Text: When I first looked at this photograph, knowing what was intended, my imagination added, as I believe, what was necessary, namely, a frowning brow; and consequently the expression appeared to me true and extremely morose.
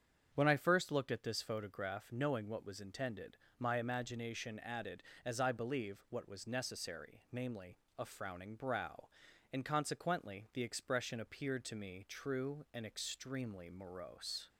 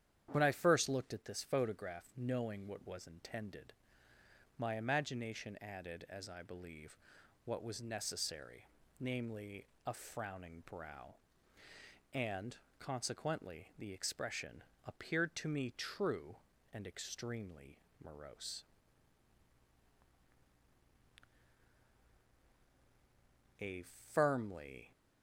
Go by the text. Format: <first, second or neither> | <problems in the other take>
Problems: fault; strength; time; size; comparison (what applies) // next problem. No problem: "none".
first | starts louder than the rest; strong; until 1.3 s; 9.5 dB; strong in the first // pauses between "and" and "consequently"; slight; at 12.5 s; 0.22 s long // pauses between "expression" and "appeared"; slight; at 14.6 s; 0.24 s long // pauses between "extremely" and "morose"; slight; at 17.7 s; 0.20 s long // goes on to say "A firmly"; from 23.5 s on; 1.3 s long